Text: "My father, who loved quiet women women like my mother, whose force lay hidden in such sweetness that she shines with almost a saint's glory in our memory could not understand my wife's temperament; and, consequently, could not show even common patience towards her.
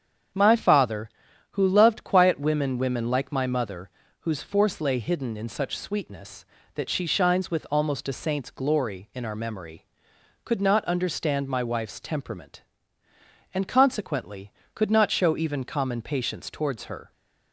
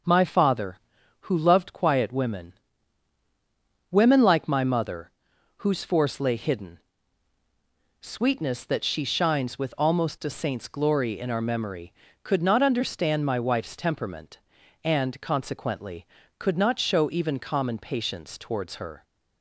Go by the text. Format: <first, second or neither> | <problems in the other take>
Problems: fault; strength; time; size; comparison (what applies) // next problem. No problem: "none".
first | starts louder than the rest; until 1.5 s; 6 dB; strong in the first // pauses between "women" and "women"; strong; at 2.5 s; 1.3 s long // skips "in such"; at 7.3 s